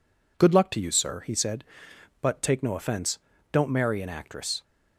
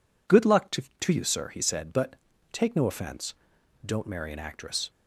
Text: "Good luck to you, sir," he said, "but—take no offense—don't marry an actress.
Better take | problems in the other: first | says "to" twice; at 0.9 s

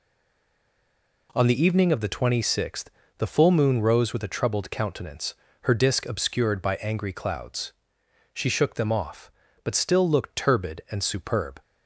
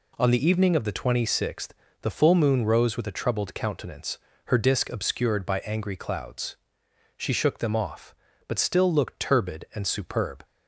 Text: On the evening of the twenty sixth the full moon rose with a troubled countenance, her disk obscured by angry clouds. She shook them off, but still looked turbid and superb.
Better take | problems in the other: second | stays silent before the first word; noticeable; until 1.2 s; 1.2 s long // pauses between "sixth" and "the"; slight; at 2.9 s; 0.28 s long; slight in the second

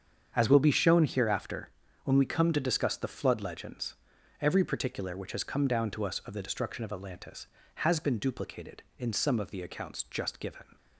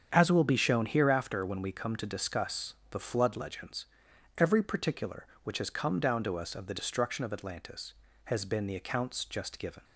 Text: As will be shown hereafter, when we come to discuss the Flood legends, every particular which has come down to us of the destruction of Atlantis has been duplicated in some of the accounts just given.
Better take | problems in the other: first | starts louder than the rest; strong; until 1.1 s; 7.5 dB; strong in the first // pauses between "discuss" and "the"; slight; at 2.7 s; 0.16 s long // skips "duplicated in some of"; at 8.6 s

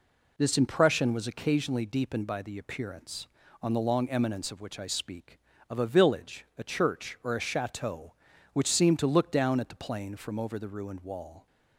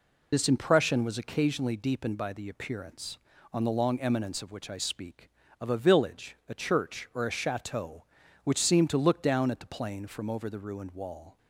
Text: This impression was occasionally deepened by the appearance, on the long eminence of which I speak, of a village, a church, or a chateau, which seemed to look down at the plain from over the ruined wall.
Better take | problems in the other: first | loses the start of "This"; at 0.3 s; 35 ms

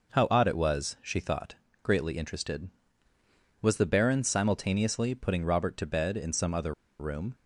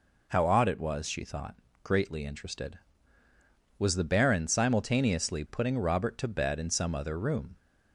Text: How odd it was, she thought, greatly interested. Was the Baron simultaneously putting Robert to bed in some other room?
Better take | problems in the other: second | pauses between "other" and "room"; slight; at 6.7 s; 0.25 s long

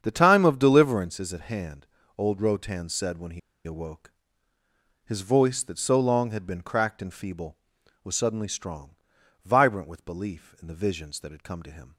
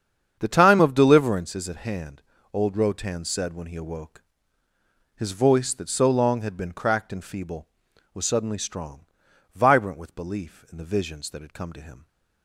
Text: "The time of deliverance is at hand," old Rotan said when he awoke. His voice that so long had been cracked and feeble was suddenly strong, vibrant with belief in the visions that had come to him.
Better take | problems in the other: second | starts louder than the rest; strong; until 1.0 s; 8 dB; strong in the second // pauses between "he" and "awoke"; slight; at 3.3 s; 0.26 s long

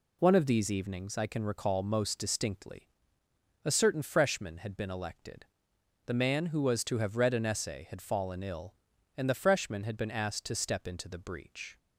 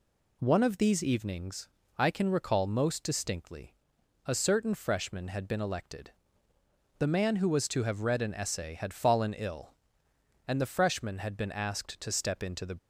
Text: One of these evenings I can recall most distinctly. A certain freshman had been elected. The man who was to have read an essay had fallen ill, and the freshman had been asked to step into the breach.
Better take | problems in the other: first | pauses between "evenings" and "I"; slight; at 1.6 s; 0.30 s long // stops before "breach"; at 12.7 s

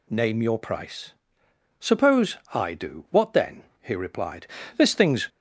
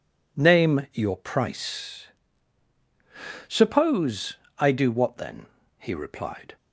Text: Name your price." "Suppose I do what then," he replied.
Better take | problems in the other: second | pauses between "Suppose" and "I"; slight; at 2.3 s; 0.16 s long; slight in the second // goes on to say "This thing's"; from 4.7 s on; 0.50 s long

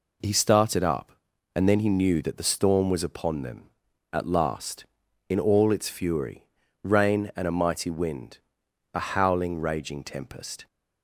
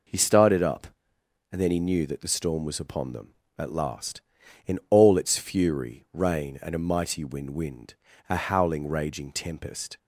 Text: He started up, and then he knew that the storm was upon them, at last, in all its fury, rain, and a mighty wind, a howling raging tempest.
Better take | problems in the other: first | says "wind" twice; at 7.4 s

